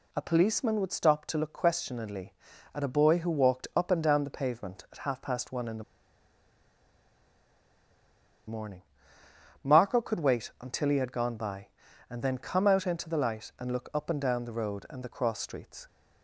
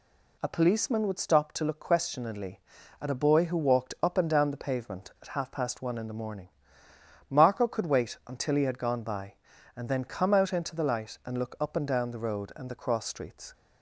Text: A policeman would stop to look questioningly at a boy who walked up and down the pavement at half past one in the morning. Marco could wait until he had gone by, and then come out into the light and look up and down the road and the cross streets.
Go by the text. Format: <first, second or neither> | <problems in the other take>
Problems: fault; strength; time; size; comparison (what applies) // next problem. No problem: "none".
second | pauses between "the" and "morning"; strong; at 5.8 s; 2.6 s long